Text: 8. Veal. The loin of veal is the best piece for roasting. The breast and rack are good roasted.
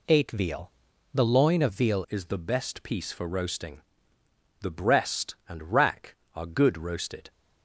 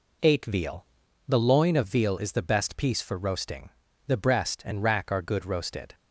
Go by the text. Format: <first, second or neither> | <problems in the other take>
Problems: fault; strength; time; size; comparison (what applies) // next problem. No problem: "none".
second | changes voice at "is"; from 2.0 s on; 5.3 s long